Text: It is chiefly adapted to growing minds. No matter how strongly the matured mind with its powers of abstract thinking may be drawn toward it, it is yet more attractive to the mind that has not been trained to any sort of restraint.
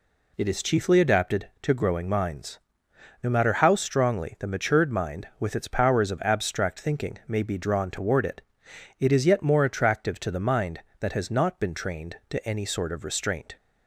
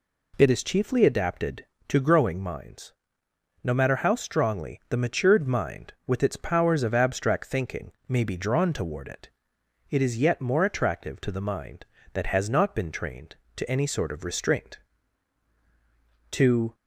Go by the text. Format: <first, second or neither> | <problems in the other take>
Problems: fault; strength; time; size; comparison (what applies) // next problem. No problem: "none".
first | pauses between "thinking" and "may"; slight; at 7.9 s; 0.16 s long // goes on to say "To"; slight; from 16.3 s on; 0.42 s long